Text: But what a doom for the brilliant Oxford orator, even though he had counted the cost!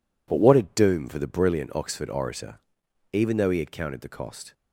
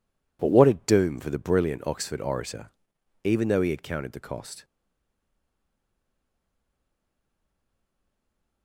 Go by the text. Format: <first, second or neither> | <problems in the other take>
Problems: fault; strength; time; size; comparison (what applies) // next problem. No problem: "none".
first | stays silent after the last word; strong; from 4.6 s on; 4.0 s long